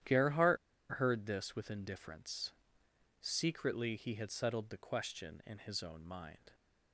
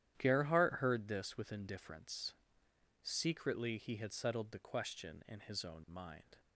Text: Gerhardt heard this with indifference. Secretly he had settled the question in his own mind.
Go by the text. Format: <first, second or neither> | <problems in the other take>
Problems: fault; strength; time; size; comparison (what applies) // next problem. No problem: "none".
second | starts louder than the rest; strong; until 1.4 s; 11 dB; strong in the second // pauses between "Gerhardt" and "heard"; at 0.5 s; 0.36 s long